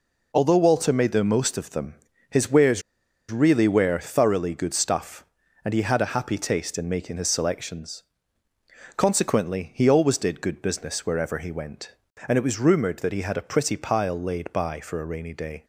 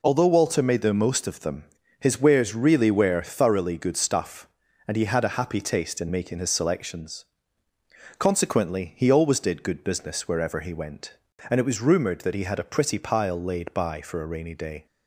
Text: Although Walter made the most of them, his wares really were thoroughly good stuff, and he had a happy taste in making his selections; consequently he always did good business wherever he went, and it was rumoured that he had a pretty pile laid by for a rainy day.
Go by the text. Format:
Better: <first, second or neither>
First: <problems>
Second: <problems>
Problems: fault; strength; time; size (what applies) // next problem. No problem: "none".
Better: second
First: pauses between "wares" and "really"; noticeable; at 2.8 s; 0.49 s long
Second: none